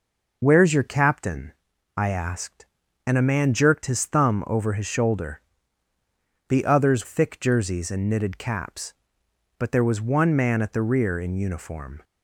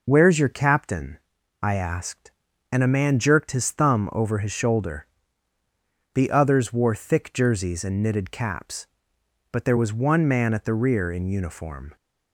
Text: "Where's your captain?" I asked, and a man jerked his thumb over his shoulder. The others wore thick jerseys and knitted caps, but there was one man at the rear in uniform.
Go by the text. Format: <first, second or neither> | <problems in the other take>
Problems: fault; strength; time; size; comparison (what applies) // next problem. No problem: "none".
second | skips "wore"; at 7.0 s